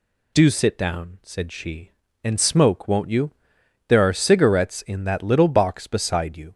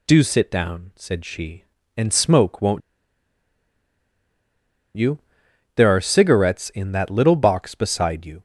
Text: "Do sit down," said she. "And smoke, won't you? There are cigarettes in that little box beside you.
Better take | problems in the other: first | pauses between "won't" and "you"; strong; at 2.8 s; 2.1 s long

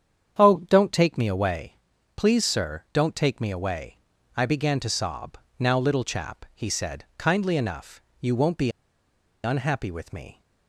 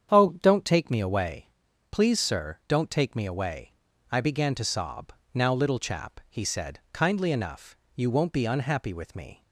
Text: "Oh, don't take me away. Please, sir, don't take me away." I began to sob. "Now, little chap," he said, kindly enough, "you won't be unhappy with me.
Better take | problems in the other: second | starts louder than the rest; strong; until 1.4 s; 8.5 dB; strong in the second // pauses between "be" and "unhappy"; noticeable; at 8.6 s; 0.74 s long

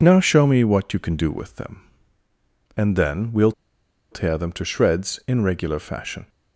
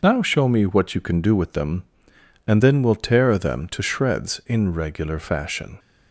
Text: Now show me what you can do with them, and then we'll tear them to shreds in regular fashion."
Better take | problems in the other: second | pauses between "we'll" and "tear"; noticeable; at 3.5 s; 0.59 s long

